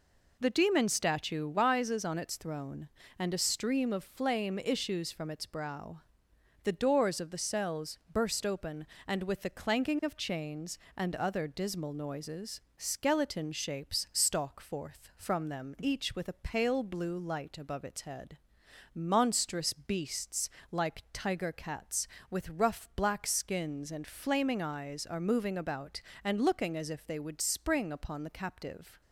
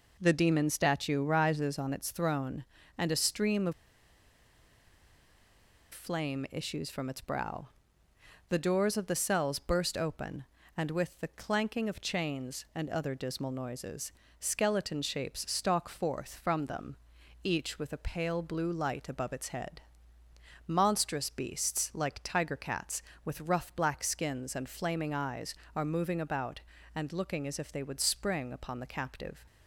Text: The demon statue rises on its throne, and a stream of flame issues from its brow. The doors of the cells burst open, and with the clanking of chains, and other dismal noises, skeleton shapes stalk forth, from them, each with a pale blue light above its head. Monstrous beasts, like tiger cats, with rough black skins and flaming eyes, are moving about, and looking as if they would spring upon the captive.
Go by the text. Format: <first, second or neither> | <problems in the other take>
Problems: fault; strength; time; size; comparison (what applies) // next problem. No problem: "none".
first | pauses between "of" and "flame"; strong; at 3.7 s; 2.2 s long